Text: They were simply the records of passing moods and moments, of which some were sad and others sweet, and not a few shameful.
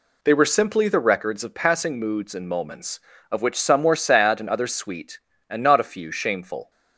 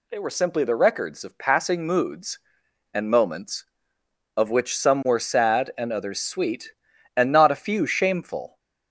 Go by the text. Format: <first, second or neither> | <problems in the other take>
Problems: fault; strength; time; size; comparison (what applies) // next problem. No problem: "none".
neither | none